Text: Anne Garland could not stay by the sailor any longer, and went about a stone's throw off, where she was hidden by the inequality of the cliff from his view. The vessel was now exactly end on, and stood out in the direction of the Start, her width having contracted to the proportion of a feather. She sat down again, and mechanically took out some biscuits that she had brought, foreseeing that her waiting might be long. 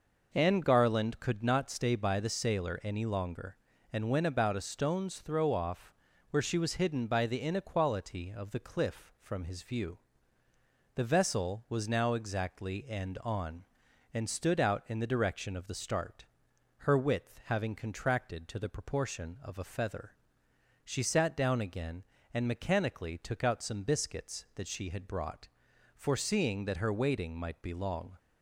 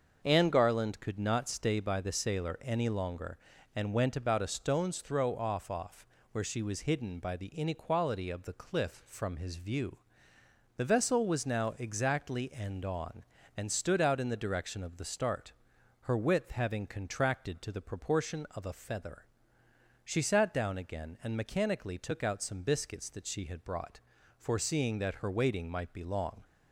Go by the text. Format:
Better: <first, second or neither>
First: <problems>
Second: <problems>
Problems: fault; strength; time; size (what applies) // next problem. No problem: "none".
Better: first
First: none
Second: starts louder than the rest; until 1.2 s; 6.5 dB // says "off" twice; at 5.7 s